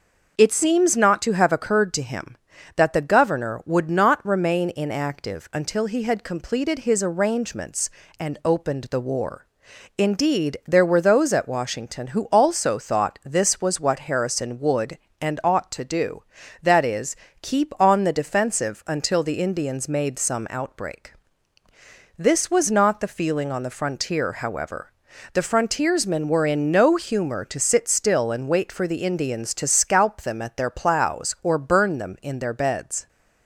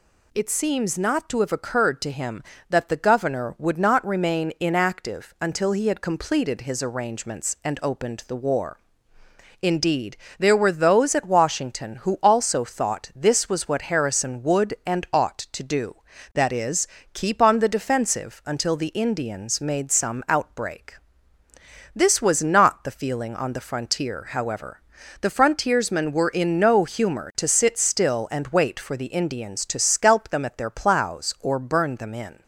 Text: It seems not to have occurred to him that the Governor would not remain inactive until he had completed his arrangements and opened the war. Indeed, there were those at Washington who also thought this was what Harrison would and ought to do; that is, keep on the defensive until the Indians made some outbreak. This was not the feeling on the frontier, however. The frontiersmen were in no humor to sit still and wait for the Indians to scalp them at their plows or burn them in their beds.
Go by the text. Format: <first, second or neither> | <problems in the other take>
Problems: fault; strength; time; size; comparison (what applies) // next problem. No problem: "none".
first | stops before "their beds"; at 32.4 s